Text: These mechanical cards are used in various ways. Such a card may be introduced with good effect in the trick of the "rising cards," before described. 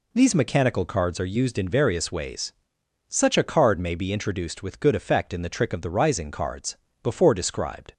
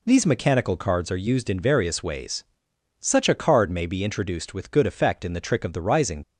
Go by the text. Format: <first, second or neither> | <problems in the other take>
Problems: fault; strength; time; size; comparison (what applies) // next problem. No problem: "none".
first | stops before "cards before described"; at 6.2 s